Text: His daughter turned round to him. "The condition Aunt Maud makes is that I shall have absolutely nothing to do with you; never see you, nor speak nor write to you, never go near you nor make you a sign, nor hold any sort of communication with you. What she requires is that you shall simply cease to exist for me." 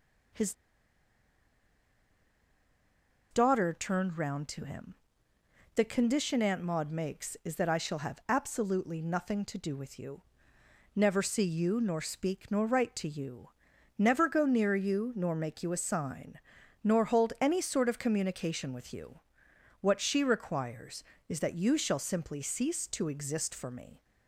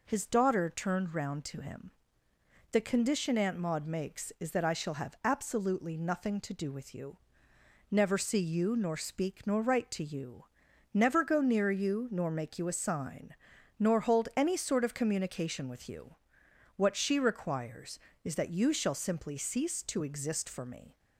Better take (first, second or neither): second